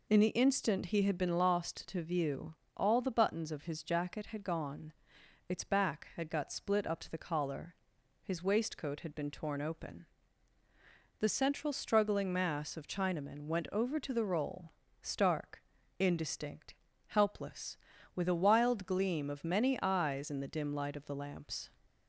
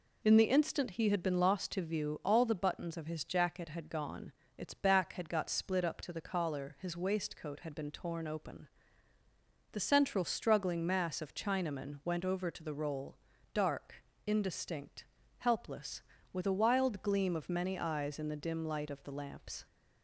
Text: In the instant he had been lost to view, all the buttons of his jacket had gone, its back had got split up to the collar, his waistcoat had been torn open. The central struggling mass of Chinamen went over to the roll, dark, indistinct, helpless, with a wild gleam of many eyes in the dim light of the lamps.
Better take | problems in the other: second | says "stark" for "dark"; at 15.0 s

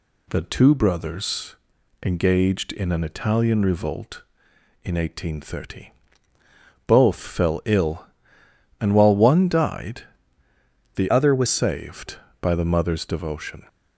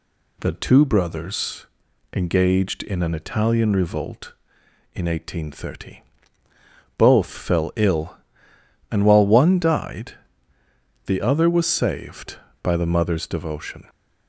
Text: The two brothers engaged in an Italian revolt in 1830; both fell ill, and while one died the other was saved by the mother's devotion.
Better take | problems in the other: second | pauses between "brothers" and "engaged"; noticeable; at 1.5 s; 0.48 s long; noticeable in the second // pauses between "died" and "the"; noticeable; at 10.0 s; 0.94 s long; noticeable in the second // changes voice from "other" to "was"; from 11.0 to 11.4 s; 0.4 s long

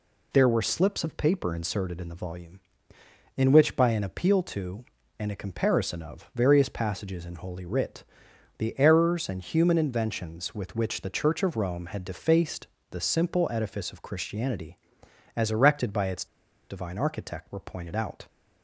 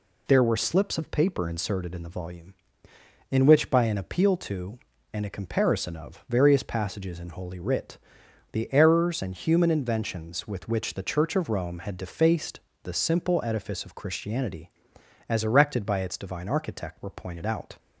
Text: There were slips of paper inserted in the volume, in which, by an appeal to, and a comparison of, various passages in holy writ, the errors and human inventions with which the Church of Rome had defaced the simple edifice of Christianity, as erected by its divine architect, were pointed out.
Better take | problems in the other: second | pauses between "defaced" and "the"; slight; at 12.6 s; 0.24 s long; slight in the second // pauses between "its" and "divine"; at 16.2 s; 0.44 s long

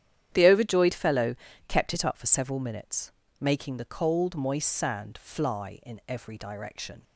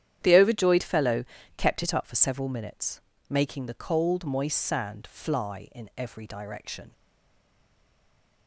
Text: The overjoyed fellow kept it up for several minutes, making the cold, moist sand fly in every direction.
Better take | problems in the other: first | starts louder than the rest; strong; until 1.2 s; 10 dB; strong in the first // pauses between "fellow" and "kept"; slight; at 1.2 s; 0.32 s long; slight in the first // stays silent after the last word; noticeable; from 6.9 s on; 1.5 s long

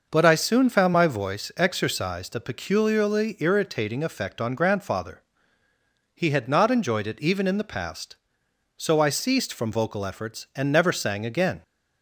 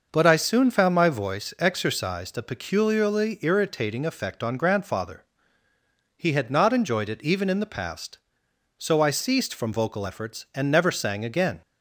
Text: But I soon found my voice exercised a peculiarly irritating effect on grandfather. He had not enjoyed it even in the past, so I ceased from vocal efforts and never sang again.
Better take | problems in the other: neither | none

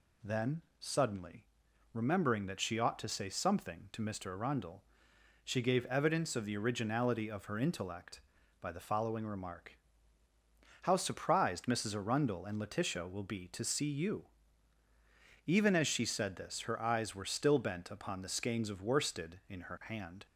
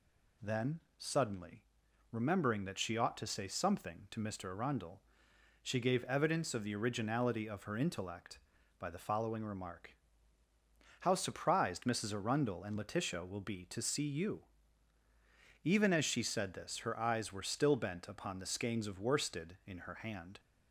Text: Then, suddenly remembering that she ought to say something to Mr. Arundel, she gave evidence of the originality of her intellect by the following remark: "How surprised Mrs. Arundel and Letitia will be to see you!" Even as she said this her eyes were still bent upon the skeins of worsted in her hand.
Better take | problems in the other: neither | pauses between "suddenly" and "remembering"; noticeable; the same in both

